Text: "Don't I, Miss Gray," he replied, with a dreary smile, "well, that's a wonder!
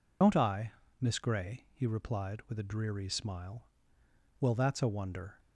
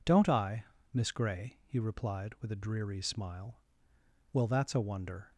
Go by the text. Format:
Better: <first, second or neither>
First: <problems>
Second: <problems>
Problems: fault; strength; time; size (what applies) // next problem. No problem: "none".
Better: second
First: loses the start of "Don't"; at 0.2 s; 125 ms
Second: none